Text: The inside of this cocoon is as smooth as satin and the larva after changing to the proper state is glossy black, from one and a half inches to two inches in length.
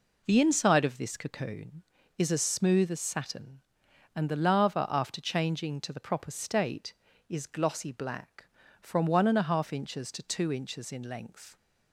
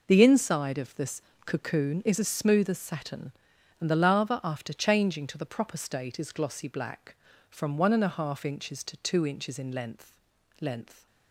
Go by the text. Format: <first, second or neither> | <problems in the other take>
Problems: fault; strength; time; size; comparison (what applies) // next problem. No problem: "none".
first | pauses between "this" and "cocoon"; slight; at 1.2 s; 0.23 s long // says "length" twice; at 10.5 s